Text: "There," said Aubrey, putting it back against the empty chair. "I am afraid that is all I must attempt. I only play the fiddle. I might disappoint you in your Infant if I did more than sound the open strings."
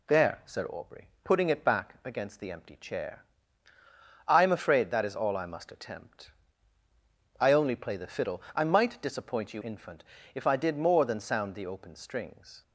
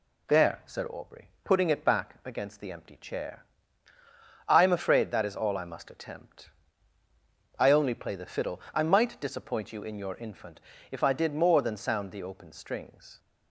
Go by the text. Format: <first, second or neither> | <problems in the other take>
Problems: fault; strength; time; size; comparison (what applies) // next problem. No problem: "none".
second | skips "in your"; at 9.6 s // pauses between "Infant" and "if"; slight; at 10.0 s; 0.30 s long; slight in the second